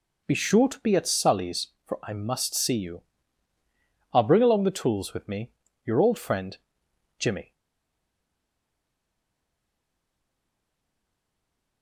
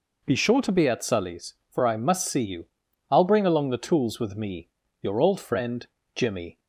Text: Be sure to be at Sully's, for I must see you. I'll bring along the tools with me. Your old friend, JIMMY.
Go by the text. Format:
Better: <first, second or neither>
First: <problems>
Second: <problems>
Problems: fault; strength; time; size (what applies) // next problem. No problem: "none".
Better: second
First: stays silent after the last word; strong; from 7.5 s on; 4.3 s long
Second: none